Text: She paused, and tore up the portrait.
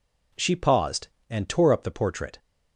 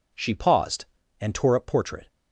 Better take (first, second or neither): first